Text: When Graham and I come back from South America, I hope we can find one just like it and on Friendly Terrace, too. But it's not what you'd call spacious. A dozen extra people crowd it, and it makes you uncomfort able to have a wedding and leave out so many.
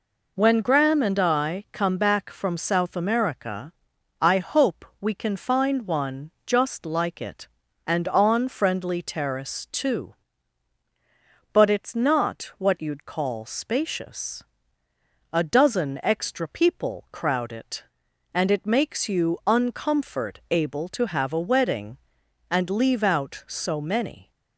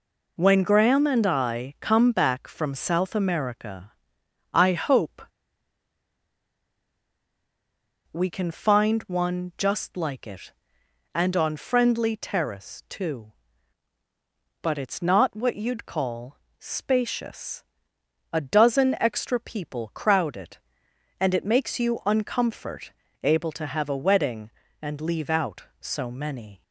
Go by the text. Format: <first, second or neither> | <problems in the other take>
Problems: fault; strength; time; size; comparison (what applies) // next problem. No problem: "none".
first | pauses between "hope" and "we"; strong; at 5.2 s; 2.9 s long // pauses between "call" and "spacious"; slight; at 16.3 s; 0.24 s long // pauses between "uncomfort" and "able"; slight; at 22.9 s; 0.34 s long